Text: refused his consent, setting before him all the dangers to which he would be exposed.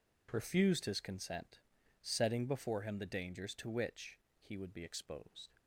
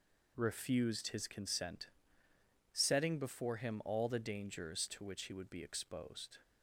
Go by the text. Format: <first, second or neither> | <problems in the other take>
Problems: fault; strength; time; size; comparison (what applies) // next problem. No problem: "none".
second | skips "all"; at 2.9 s // pauses between "which" and "he"; slight; at 4.1 s; 0.24 s long